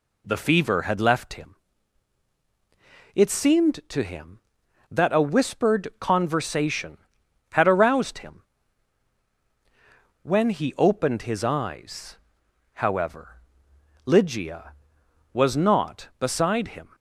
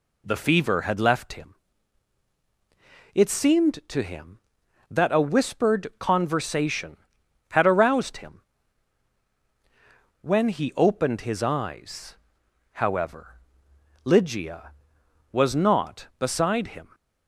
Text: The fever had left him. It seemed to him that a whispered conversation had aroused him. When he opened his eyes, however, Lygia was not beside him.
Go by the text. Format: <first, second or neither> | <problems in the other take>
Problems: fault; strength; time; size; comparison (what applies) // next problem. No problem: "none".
neither | none